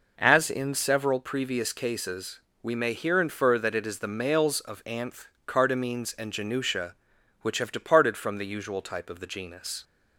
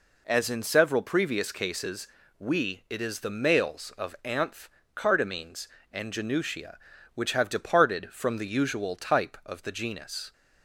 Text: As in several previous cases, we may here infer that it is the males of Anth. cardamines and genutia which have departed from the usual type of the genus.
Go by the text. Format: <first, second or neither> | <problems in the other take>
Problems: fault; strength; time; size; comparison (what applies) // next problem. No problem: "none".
first | skips "may here infer that"; at 2.8 s